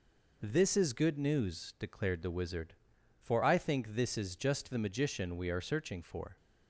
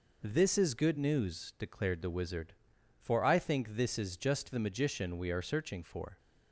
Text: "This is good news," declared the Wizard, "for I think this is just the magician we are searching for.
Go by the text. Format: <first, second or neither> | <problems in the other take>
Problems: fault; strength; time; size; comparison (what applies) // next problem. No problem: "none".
neither | none